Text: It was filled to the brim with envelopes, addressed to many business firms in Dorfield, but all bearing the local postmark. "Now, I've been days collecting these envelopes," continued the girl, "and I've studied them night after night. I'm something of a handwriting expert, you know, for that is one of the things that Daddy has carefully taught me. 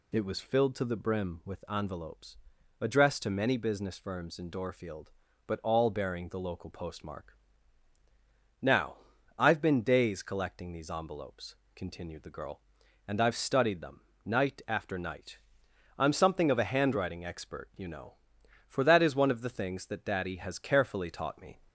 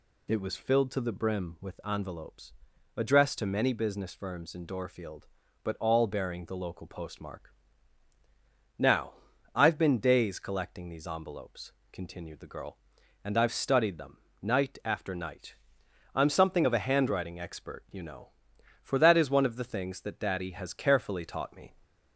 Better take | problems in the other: neither | pauses between "them" and "night"; slight; the same in both

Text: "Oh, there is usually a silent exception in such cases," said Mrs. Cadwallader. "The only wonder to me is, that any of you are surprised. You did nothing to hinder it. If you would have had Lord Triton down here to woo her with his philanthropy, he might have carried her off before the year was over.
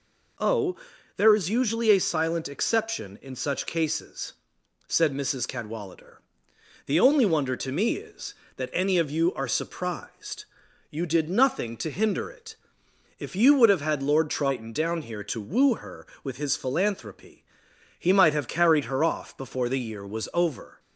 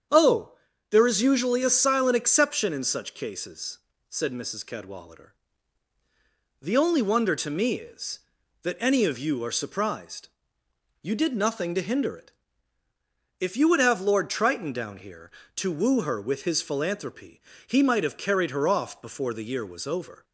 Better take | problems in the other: first | starts louder than the rest; strong; until 1.4 s; 7.5 dB // skips "had"; at 13.9 s

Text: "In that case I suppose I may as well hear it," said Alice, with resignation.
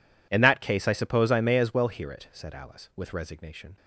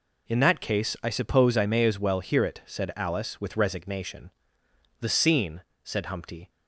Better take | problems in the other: first | goes on to say "The scene said Humpty"; from 4.9 s on; 1.5 s long

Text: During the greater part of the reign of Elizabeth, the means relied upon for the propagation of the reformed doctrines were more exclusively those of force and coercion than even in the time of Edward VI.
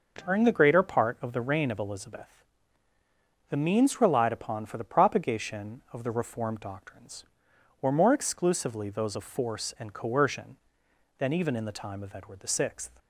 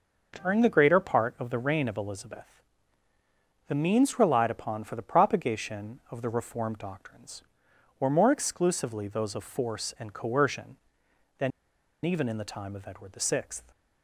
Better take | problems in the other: first | pauses between "than" and "even"; noticeable; at 11.5 s; 0.54 s long

